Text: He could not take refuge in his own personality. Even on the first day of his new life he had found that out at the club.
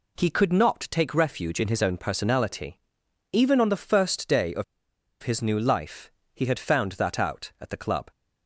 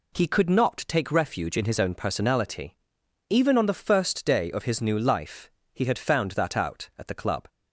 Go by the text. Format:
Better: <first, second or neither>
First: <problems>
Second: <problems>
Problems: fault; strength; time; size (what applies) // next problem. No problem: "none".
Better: second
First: pauses between "of" and "his"; noticeable; at 4.6 s; 0.59 s long // pauses between "life" and "he"; slight; at 6.0 s; 0.24 s long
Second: pauses between "life" and "he"; slight; at 5.4 s; 0.24 s long